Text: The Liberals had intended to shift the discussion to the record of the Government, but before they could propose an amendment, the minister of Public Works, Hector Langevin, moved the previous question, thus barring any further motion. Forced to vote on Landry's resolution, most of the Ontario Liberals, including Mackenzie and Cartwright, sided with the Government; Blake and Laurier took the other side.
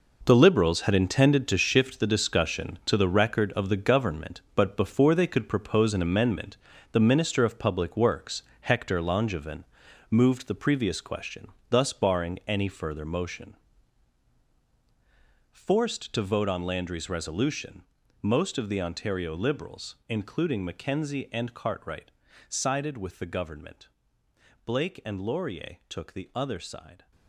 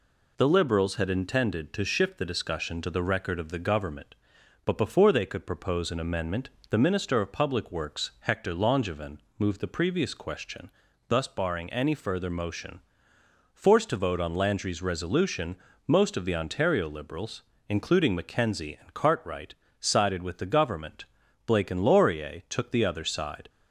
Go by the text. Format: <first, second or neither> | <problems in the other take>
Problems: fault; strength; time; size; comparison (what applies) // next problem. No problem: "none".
second | gets quieter; strong; throughout; 11 dB